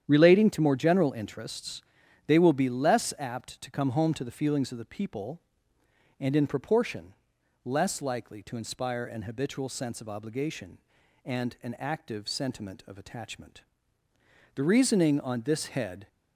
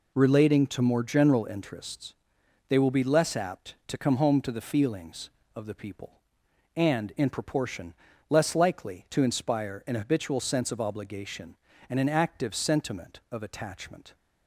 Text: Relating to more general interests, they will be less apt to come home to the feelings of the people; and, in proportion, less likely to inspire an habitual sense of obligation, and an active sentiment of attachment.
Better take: second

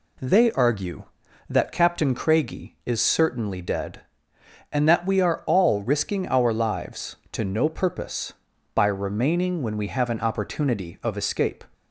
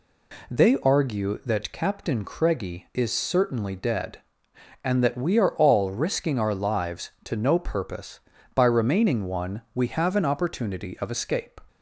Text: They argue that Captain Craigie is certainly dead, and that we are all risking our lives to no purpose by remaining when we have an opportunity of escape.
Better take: first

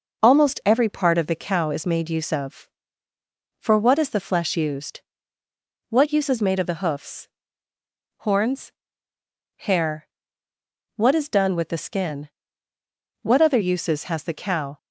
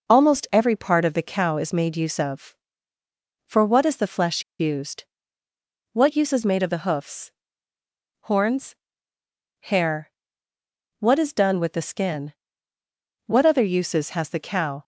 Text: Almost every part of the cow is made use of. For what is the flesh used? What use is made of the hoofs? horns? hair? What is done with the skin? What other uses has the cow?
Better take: first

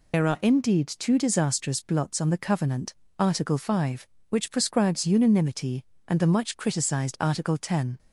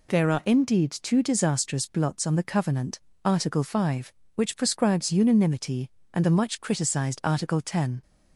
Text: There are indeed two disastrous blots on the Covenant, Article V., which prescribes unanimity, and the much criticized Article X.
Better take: second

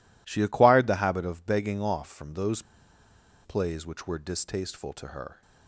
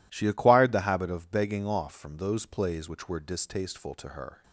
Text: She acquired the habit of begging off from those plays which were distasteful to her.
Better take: second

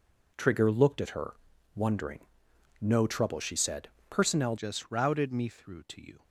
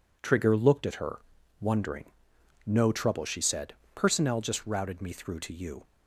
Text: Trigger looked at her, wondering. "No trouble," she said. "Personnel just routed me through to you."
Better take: second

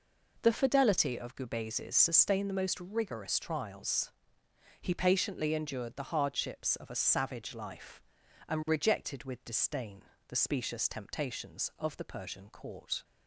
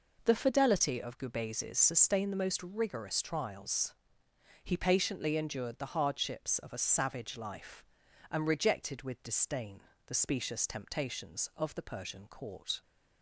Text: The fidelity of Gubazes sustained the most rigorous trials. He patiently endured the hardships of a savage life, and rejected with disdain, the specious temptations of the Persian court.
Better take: neither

